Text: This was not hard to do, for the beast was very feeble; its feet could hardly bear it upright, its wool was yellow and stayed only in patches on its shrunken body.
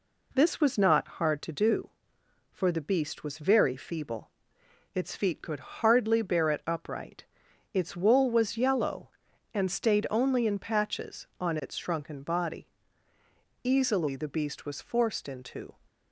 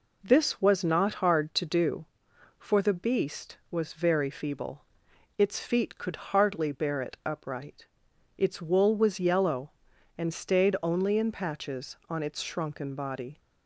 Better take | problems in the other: second | goes on to say "Easily the beast was forced into"; strong; from 13.6 s on; 2.1 s long

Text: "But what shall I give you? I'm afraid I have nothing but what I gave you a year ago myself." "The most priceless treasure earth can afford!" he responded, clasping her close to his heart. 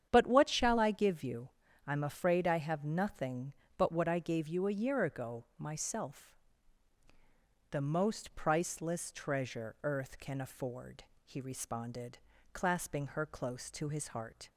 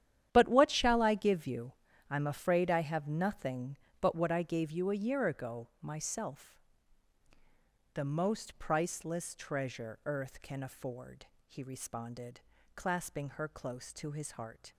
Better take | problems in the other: first | gets quieter; strong; throughout; 13.5 dB // starts louder than the rest; strong; until 1.3 s; 10.5 dB; strong in the first

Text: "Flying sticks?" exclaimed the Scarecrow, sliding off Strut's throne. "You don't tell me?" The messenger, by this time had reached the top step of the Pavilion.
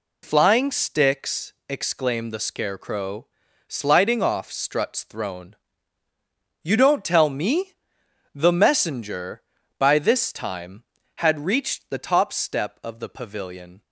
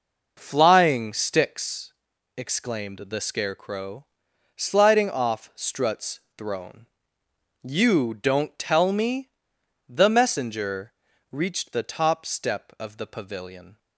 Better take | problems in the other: first | pauses between "Strut's" and "throne"; slight; at 6.1 s; 0.16 s long // skips "by this time had"; at 11.1 s

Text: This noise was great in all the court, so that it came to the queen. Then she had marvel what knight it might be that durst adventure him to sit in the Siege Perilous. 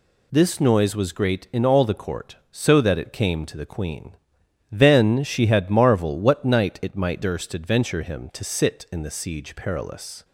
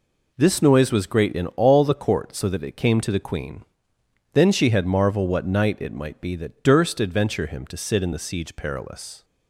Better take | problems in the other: second | skips "be that"; at 7.2 s

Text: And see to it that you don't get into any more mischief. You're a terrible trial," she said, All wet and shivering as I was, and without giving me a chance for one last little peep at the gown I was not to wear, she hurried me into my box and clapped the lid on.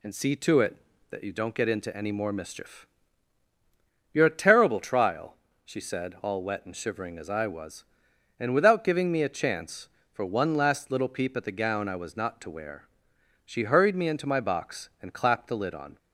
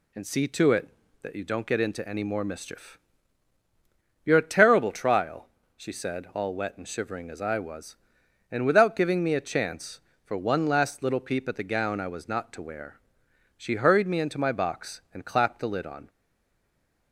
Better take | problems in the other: first | stays silent after the last word; from 16.0 s on; 1.1 s long

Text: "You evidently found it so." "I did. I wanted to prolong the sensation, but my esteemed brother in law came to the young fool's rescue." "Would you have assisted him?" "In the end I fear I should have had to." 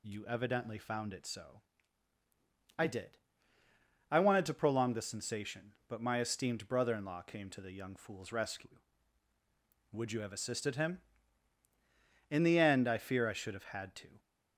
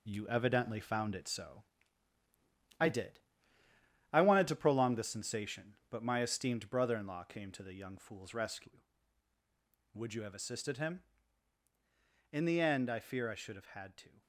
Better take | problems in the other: first | gets quieter; throughout; 6.5 dB

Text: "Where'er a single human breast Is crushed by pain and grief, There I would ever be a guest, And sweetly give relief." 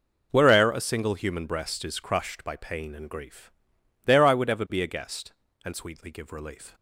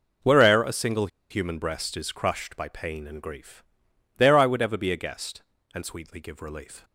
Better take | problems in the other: first | pauses between "single" and "human"; slight; at 1.0 s; 0.22 s long

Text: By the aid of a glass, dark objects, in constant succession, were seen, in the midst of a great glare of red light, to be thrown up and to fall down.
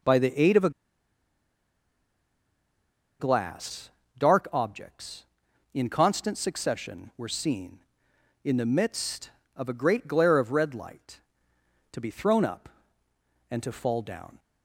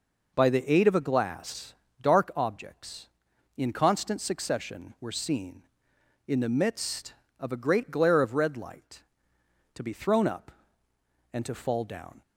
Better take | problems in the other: second | pauses between "a" and "glass"; strong; at 0.6 s; 2.4 s long

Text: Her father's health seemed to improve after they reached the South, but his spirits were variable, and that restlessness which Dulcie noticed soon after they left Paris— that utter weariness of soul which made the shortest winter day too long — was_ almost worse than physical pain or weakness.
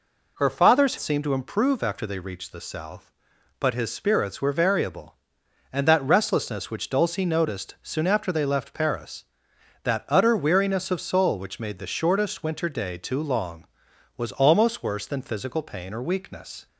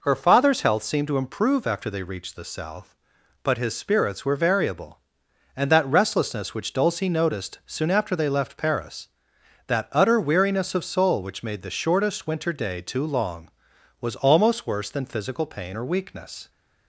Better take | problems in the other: second | skips "health"; at 0.9 s

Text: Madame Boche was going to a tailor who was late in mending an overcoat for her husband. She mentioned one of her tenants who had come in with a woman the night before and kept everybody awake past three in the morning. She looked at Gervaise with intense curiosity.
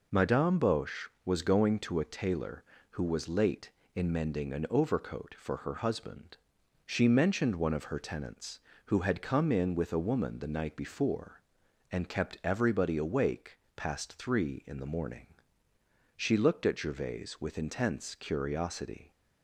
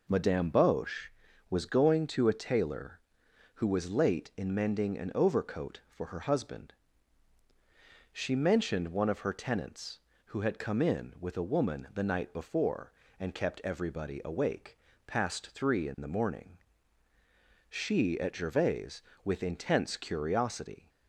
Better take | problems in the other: first | pauses between "awake" and "past"; slight; at 14.7 s; 0.28 s long; slight in the first // skips "looked"; at 18.1 s

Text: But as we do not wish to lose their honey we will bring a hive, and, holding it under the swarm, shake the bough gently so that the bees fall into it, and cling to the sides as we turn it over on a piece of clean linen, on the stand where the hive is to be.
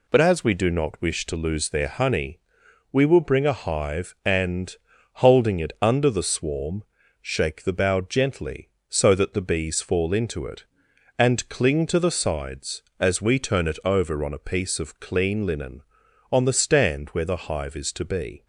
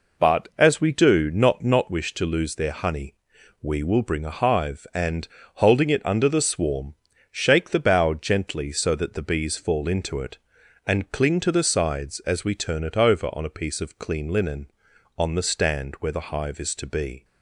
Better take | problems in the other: first | says "not" twice; at 1.6 s // pauses between "honey" and "we"; noticeable; at 3.1 s; 0.46 s long; noticeable in the first

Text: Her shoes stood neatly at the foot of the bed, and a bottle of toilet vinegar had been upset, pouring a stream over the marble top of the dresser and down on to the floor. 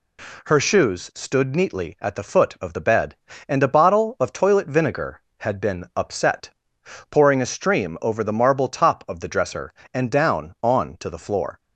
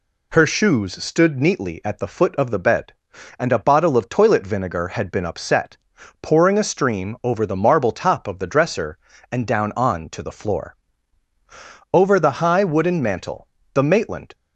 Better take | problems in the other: first | goes on to say "Over the high wooden mantel the Maitland"; strong; from 11.9 s on; 2.4 s long

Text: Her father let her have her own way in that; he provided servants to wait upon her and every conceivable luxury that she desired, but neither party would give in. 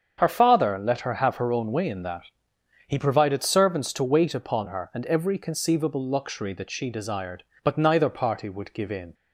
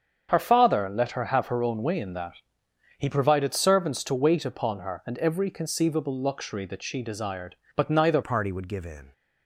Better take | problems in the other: first | starts louder than the rest; strong; until 1.3 s; 7 dB; strong in the first // changes voice at "party"; from 8.2 s on; 0.9 s long

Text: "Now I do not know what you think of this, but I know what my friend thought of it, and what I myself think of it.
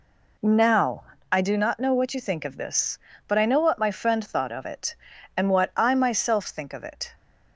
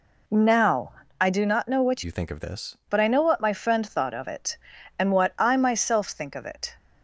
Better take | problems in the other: first | pauses between "Now" and "I"; slight; at 0.9 s; 0.28 s long; slight in the first // changes voice from "you" to "this"; from 2.0 to 2.7 s; 0.7 s long

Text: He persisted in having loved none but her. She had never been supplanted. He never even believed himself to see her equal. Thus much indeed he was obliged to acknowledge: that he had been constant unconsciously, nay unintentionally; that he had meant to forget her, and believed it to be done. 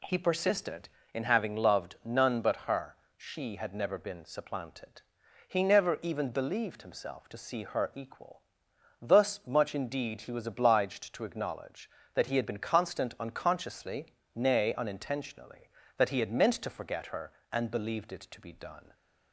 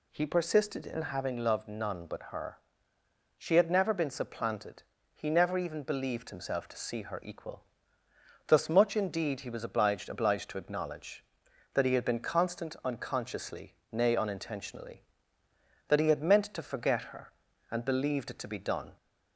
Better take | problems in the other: first | says "obliged" twice; at 10.0 s

